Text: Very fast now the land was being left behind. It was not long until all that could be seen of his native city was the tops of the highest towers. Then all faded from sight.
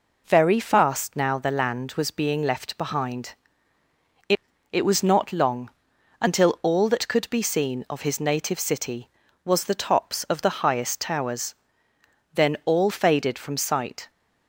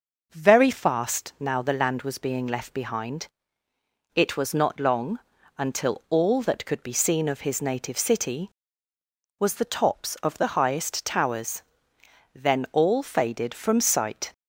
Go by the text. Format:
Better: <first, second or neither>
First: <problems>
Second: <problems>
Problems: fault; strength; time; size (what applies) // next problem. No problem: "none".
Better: second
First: says "It" twice; at 4.7 s // pauses between "long" and "until"; noticeable; at 5.6 s; 0.52 s long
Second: pauses between "long" and "until"; at 5.1 s; 0.40 s long